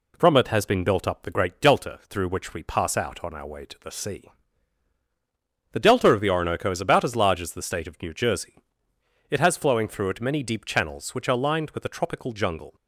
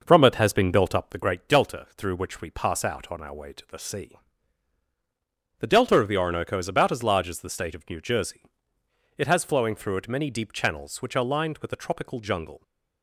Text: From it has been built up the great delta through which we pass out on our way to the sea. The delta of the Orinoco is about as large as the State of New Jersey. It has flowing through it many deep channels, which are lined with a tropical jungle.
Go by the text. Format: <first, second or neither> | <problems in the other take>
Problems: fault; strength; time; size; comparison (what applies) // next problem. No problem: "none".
first | starts louder than the rest; noticeable; until 1.3 s; 6 dB